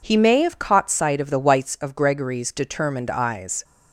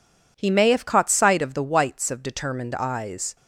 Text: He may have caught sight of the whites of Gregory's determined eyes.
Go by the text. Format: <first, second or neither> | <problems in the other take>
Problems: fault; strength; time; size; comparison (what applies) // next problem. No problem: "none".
first | skips "Gregory's"; at 2.2 s